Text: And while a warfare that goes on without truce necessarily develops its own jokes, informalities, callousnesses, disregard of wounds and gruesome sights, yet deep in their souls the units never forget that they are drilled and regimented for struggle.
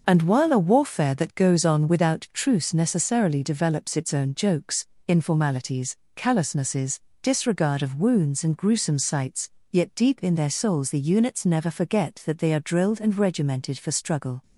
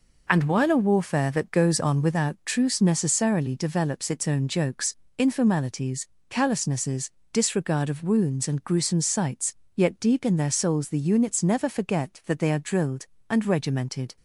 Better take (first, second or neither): first